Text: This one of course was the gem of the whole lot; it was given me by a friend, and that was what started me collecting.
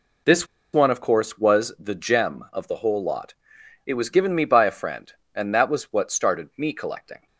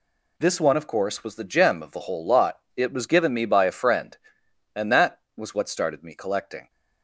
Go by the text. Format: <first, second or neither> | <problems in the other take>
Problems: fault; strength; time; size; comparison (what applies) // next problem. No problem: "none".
second | pauses between "This" and "one"; slight; at 0.4 s; 0.27 s long